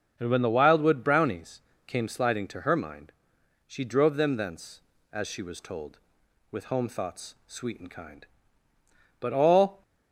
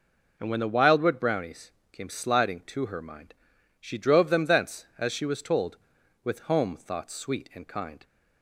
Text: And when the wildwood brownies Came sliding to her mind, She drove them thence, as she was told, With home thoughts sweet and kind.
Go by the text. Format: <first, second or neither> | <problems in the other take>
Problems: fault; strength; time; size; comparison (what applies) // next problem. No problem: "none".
second | starts louder than the rest; until 1.1 s; 6.5 dB // pauses between "brownies" and "Came"; slight; at 1.5 s; 0.26 s long; slight in the second // goes on to say "But all"; noticeable; from 9.1 s on; 0.62 s long